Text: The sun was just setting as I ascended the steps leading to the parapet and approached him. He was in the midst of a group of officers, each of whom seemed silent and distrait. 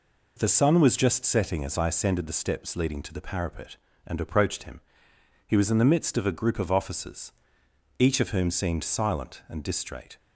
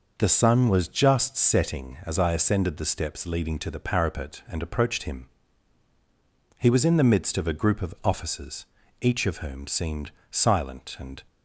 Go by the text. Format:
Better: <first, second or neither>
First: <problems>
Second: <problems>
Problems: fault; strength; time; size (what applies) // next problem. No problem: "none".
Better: first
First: none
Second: pauses between "seemed" and "silent"; slight; at 10.1 s; 0.20 s long // stops before "distrait"; at 11.2 s